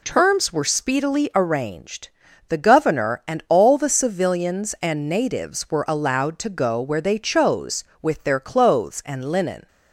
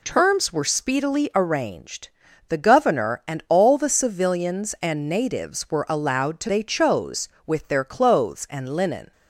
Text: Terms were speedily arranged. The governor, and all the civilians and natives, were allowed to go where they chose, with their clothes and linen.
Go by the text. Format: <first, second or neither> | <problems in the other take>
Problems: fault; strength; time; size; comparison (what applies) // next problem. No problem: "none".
first | skips "go where"; at 6.4 s